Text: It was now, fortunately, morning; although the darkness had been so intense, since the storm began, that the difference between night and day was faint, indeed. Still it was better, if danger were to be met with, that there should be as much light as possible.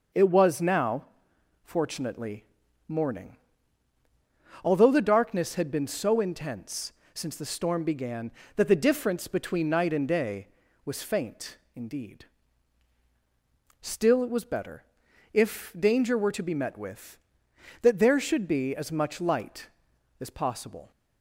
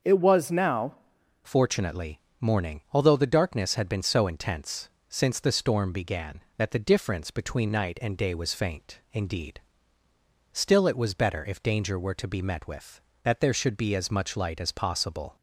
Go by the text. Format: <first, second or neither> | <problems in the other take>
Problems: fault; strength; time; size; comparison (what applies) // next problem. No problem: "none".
first | starts louder than the rest; until 1.5 s; 6 dB // changes voice at "fortunately"; from 1.4 s on; 13.9 s long